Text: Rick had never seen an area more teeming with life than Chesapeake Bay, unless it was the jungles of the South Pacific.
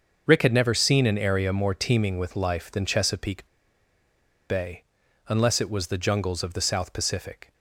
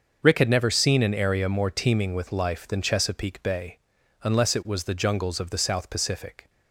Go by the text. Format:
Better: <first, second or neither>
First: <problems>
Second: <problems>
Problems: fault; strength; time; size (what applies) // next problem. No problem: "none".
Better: second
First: starts louder than the rest; until 1.3 s; 6.5 dB // pauses between "Chesapeake" and "Bay"; at 3.4 s; 1.0 s long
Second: starts louder than the rest; until 1.2 s; 6.5 dB